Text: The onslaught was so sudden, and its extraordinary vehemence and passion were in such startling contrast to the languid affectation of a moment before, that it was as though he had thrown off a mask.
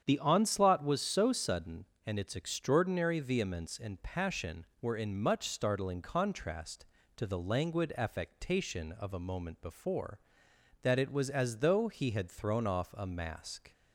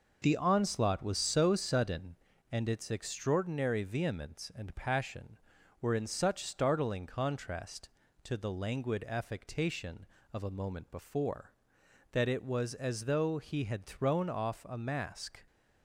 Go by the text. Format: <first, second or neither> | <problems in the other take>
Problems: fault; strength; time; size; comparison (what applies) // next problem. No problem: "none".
second | starts louder than the rest; strong; until 1.0 s; 8.5 dB // says "much" for "such"; at 5.2 s